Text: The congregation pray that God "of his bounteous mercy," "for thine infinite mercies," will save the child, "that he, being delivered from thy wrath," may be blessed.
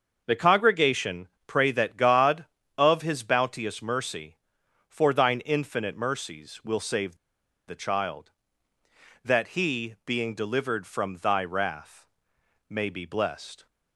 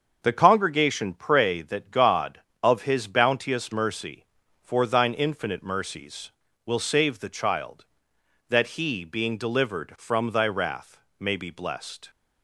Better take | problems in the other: second | starts louder than the rest; until 1.2 s; 6.5 dB; also in the second // pauses between "congregation" and "pray"; slight; at 1.2 s; 0.20 s long // pauses between "save" and "the"; noticeable; at 7.1 s; 0.51 s long

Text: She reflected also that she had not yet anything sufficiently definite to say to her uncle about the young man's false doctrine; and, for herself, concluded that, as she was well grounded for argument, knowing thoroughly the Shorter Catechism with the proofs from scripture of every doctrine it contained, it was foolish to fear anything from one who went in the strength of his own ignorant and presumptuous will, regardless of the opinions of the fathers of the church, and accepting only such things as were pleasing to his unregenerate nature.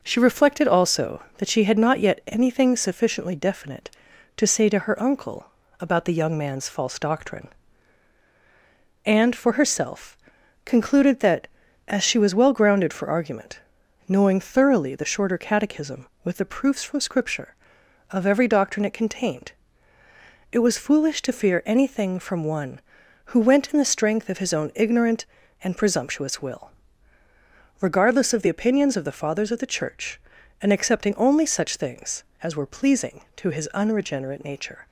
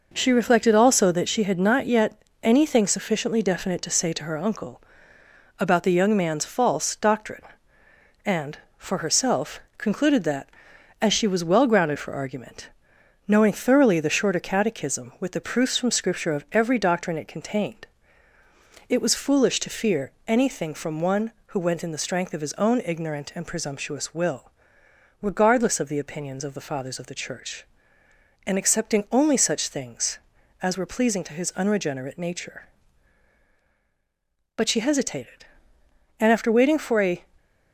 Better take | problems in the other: first | pauses between "yet" and "anything"; slight; at 2.2 s; 0.22 s long // pauses between "uncle" and "about"; noticeable; at 4.8 s; 0.78 s long; slight in the first // pauses between "fear" and "anything"; slight; at 20.1 s; 0.16 s long // goes on to say "But she hesitated and after waiting for a"; strong; from 34.5 s on; 2.6 s long

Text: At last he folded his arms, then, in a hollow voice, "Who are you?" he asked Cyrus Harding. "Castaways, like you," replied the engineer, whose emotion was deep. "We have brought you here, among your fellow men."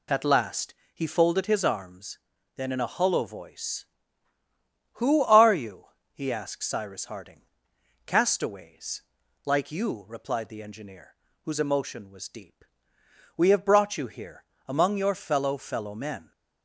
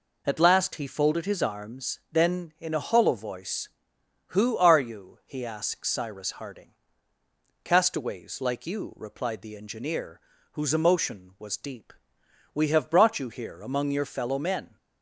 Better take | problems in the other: second | pauses between "last" and "he"; slight; at 0.7 s; 0.20 s long // says "fellow" twice; at 15.5 s

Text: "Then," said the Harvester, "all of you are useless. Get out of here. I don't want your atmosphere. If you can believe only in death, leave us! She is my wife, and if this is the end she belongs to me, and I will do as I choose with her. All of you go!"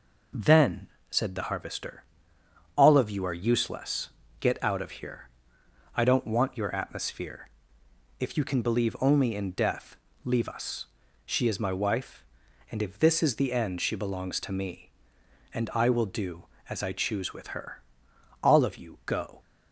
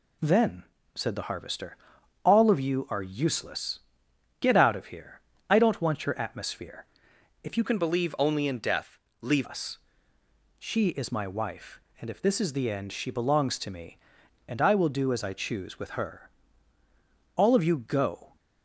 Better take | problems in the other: first | changes voice from "can" to "leave"; from 7.6 to 9.4 s; 1.8 s long

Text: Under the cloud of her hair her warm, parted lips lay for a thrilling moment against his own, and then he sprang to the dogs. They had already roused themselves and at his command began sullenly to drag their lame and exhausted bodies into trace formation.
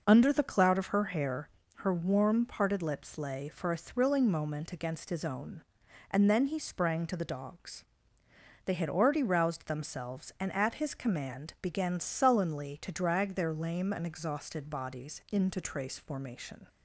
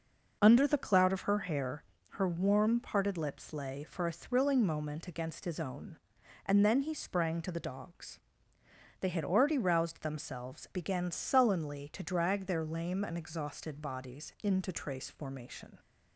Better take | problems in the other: first | pauses between "hair" and "her"; slight; at 1.8 s; 0.28 s long; slight in the first // skips "and at his command"; at 10.6 s

